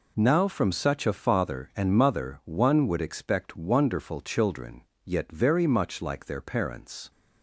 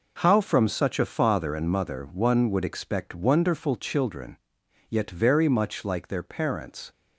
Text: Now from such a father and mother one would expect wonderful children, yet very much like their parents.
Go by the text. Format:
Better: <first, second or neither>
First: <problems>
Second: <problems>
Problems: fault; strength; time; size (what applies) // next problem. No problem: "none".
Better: first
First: none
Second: says "How" for "Now"; at 0.2 s